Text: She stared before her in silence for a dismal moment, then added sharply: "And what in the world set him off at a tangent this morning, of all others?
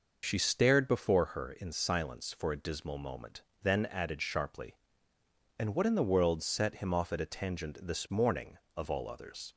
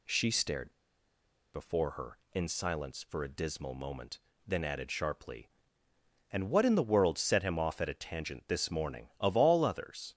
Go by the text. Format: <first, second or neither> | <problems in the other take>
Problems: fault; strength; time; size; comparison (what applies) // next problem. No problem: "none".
first | pauses between "stared" and "before"; noticeable; at 0.7 s; 0.82 s long